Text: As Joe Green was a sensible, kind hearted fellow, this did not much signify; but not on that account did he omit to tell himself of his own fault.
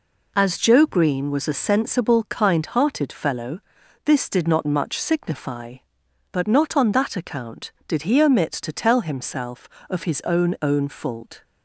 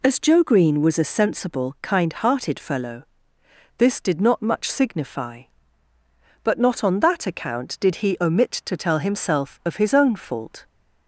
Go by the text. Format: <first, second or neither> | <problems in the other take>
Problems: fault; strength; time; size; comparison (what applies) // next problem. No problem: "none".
second | says "own" twice; at 10.5 s